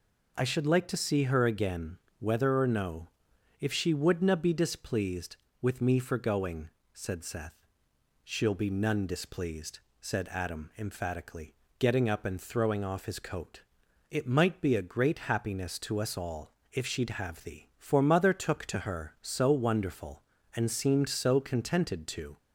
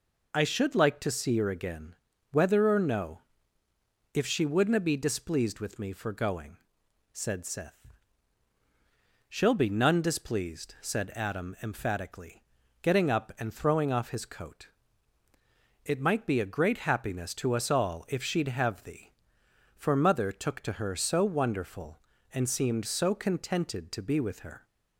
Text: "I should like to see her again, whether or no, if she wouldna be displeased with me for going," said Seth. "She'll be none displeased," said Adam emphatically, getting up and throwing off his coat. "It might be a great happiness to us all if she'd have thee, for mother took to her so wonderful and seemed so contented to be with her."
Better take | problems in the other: second | pauses between "all" and "if"; slight; at 16.5 s; 0.18 s long // stops before "be with her"; at 22.3 s

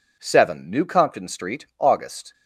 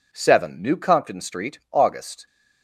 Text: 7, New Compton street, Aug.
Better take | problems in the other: neither | none

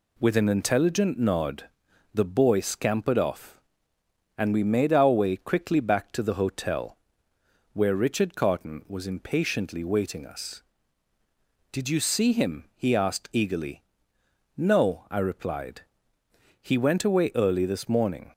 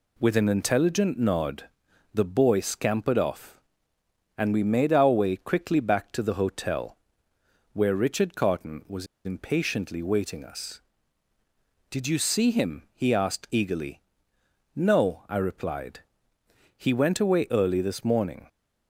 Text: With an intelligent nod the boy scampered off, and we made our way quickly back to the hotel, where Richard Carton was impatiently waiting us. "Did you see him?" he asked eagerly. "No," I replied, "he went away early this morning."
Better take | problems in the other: first | pauses between "nod" and "the"; at 1.6 s; 0.42 s long; also in the first // pauses between "was" and "impatiently"; slight; at 9.0 s; 0.19 s long

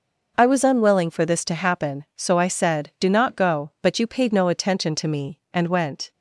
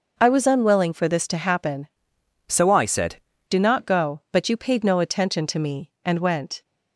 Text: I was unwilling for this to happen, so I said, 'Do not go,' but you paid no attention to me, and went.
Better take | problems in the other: first | changes voice from "so" to "said"; from 2.4 to 3.1 s; 0.7 s long

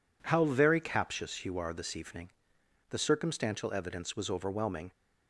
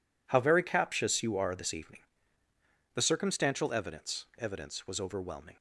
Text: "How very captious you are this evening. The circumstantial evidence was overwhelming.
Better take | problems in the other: first | says "evidence" twice; at 4.3 s

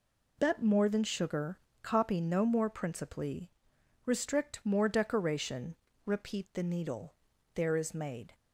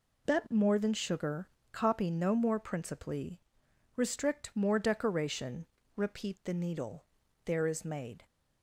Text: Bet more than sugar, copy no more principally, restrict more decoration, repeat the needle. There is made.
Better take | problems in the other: neither | none

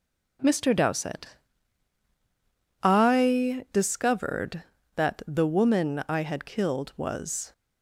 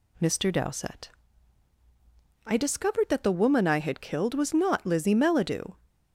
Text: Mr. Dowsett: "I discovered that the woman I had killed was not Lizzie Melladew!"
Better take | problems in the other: second | stops before "not Lizzie Melladew"; at 7.5 s

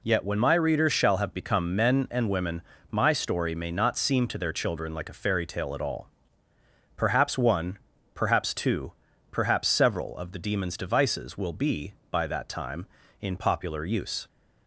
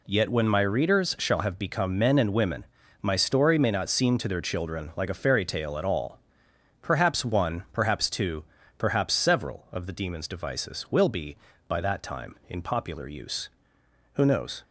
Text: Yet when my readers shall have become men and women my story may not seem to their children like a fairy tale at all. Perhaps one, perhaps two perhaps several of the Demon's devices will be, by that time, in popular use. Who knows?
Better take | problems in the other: second | pauses between "women" and "my"; slight; at 2.6 s; 0.32 s long; also in the second // pauses between "two" and "perhaps"; slight; at 8.9 s; 0.36 s long; slight in the second // stops before "Who knows"; at 14.2 s

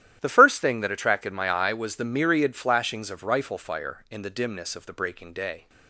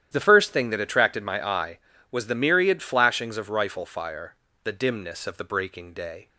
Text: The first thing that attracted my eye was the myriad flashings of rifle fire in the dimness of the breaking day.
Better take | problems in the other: first | starts louder than the rest; strong; until 1.1 s; 11 dB; strong in the first // skips "in"; at 4.4 s

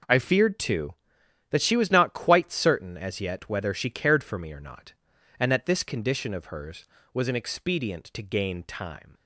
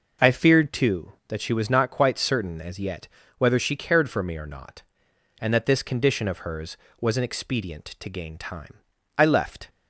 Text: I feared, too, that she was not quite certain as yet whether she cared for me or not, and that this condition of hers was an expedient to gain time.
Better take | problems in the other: first | pauses between "yet" and "whether"; slight; at 3.0 s; 0.30 s long // goes on to say "I left"; from 9.1 s on; 0.54 s long

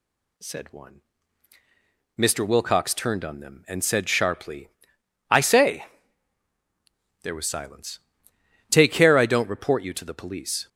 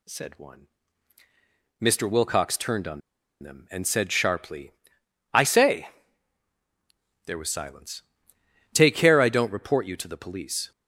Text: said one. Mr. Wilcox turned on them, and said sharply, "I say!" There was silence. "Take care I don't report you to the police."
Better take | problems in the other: first | pauses between "on" and "them"; at 3.0 s; 0.42 s long

